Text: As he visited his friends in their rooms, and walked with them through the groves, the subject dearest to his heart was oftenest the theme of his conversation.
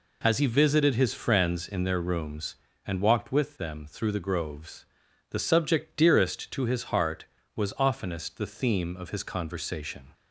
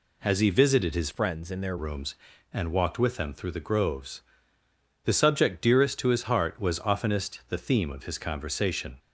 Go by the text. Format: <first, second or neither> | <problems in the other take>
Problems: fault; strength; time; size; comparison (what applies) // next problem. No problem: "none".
first | changes voice from "friends" to "their"; from 1.1 to 1.7 s; 0.6 s long